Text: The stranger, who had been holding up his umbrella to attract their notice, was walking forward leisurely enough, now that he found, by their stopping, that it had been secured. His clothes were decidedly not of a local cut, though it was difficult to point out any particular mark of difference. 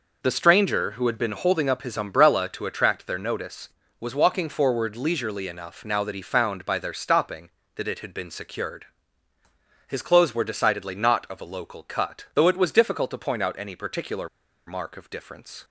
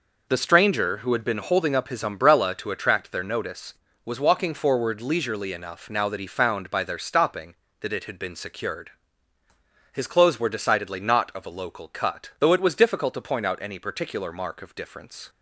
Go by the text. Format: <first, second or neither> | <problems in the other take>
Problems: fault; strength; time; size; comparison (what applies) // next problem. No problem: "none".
second | pauses between "particular" and "mark"; at 14.2 s; 0.38 s long